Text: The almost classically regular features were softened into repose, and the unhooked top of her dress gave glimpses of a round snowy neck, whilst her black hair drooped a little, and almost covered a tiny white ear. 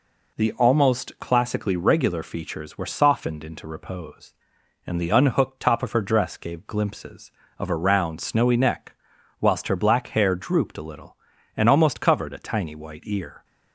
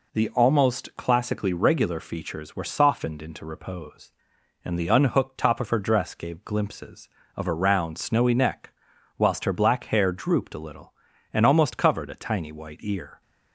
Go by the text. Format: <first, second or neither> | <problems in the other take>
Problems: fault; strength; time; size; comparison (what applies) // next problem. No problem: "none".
neither | none